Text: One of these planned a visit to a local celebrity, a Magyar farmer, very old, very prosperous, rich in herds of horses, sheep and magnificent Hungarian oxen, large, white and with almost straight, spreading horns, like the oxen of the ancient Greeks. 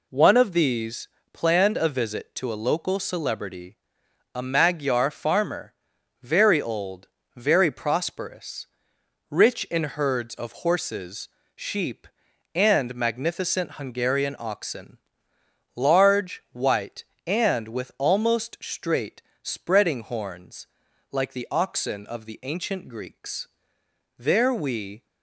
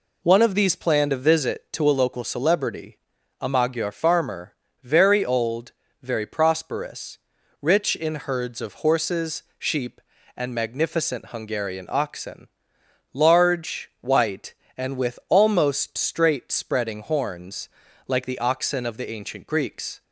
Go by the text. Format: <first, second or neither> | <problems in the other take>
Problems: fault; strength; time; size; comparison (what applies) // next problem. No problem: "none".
second | pauses between "these" and "planned"; slight; at 1.0 s; 0.24 s long // goes on to say "There we"; noticeable; from 24.1 s on; 0.88 s long